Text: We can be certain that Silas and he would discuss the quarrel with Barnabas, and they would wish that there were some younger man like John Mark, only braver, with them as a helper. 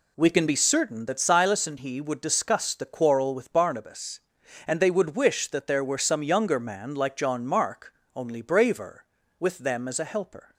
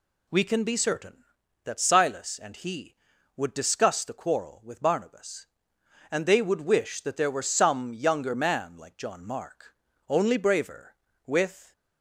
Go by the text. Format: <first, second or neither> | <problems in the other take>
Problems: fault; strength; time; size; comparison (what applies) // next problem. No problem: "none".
first | stops before "them as a helper"; at 11.7 s